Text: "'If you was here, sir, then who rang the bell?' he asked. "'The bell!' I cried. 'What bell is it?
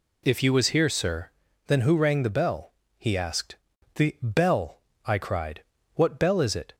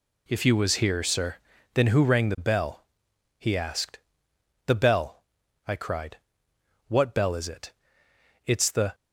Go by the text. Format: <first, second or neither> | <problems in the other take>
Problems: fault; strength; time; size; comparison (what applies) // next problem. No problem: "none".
first | goes on to say "It's the"; from 8.4 s on; 0.50 s long